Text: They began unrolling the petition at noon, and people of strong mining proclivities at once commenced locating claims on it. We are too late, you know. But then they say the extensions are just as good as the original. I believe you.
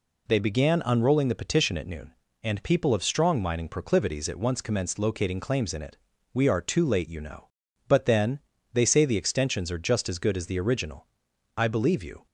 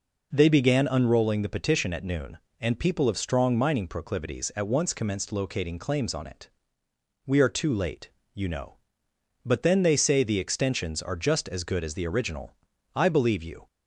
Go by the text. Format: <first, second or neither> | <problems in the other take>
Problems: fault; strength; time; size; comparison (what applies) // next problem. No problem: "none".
second | says "in" for "on"; at 5.7 s // pauses between "then" and "they"; slight; at 8.3 s; 0.34 s long